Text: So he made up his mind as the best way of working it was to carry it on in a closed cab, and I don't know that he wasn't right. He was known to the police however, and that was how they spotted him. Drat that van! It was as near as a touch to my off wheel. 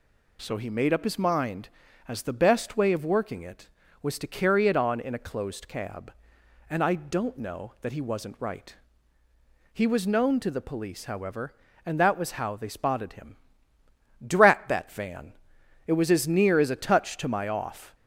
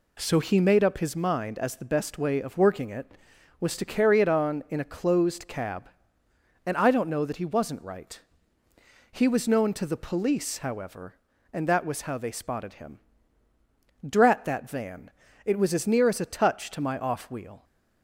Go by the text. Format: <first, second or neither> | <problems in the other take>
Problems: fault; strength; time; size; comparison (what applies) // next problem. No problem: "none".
second | stops before "wheel"; at 17.9 s